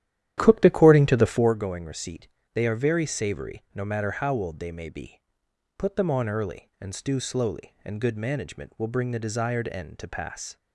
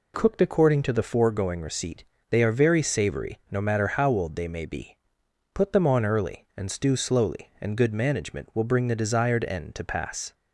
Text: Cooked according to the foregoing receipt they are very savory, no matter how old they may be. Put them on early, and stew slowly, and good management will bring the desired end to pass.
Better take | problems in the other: second | starts louder than the rest; strong; until 1.6 s; 11.5 dB // pauses between "receipt" and "they"; slight; at 2.2 s; 0.24 s long; slight in the second

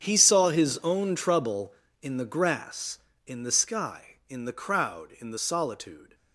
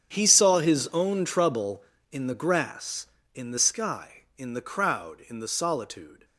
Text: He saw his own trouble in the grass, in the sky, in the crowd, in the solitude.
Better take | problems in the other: neither | starts louder than the rest; strong; the same in both

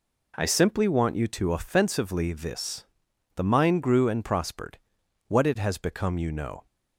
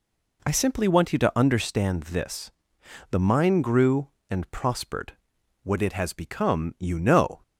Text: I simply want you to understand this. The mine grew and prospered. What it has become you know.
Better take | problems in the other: second | says "offensively" for "understand"; at 1.5 s

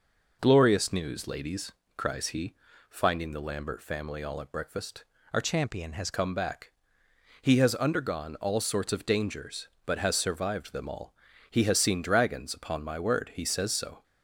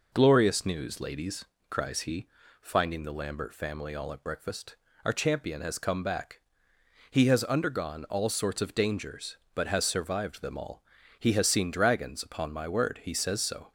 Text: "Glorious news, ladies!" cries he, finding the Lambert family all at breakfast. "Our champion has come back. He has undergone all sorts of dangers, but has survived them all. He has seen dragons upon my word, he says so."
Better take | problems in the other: second | changes voice from "champion" to "has"; from 5.4 to 6.1 s; 0.7 s long

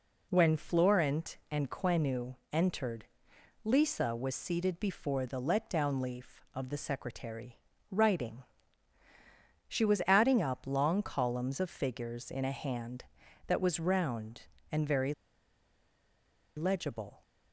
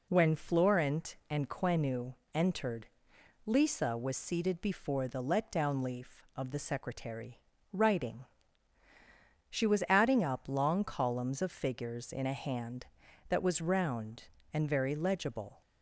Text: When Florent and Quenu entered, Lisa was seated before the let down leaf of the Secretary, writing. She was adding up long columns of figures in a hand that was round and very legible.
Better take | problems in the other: second | pauses between "Quenu" and "entered"; slight; at 2.3 s; 0.18 s long; slight in the second // pauses between "very" and "legible"; strong; at 15.1 s; 1.4 s long

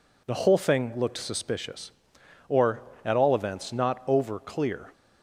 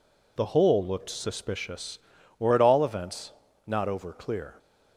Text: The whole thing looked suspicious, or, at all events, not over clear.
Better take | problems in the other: first | skips "thing"; at 0.8 s

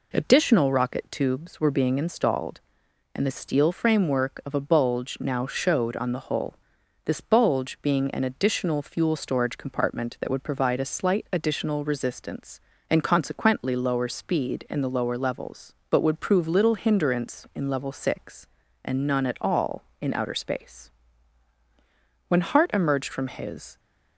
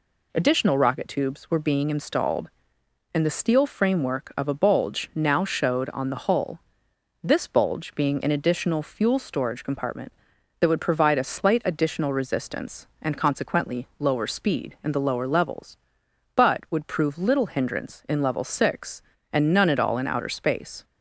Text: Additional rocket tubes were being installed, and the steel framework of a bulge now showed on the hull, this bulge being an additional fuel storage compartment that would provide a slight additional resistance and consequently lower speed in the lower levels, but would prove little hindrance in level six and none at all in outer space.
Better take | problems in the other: second | goes on to say "When Hart emerged from his"; from 22.2 s on; 1.5 s long

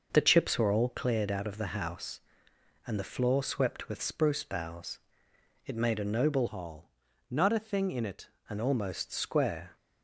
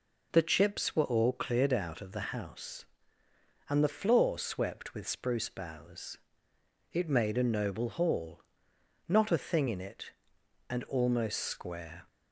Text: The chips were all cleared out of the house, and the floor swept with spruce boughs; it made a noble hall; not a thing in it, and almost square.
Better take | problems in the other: second | changes voice from "hall" to "it"; from 6.4 to 8.2 s; 1.8 s long

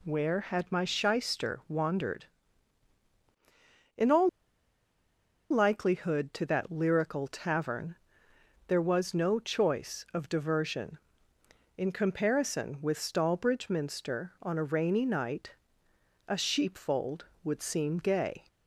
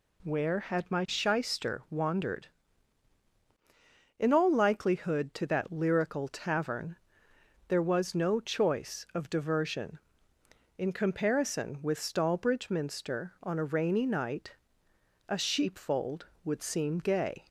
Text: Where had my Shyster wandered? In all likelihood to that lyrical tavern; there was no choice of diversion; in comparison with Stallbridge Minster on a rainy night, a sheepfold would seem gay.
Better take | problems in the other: second | pauses between "all" and "likelihood"; at 4.2 s; 1.2 s long

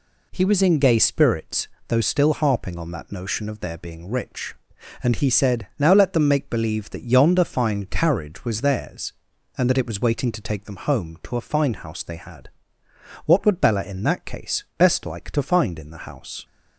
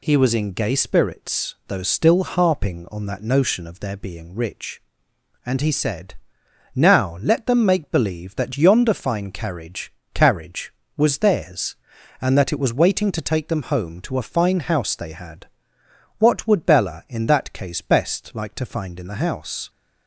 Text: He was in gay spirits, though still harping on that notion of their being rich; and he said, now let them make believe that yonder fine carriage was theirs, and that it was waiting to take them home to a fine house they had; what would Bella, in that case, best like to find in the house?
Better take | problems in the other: first | says "carriage" twice; at 10.1 s

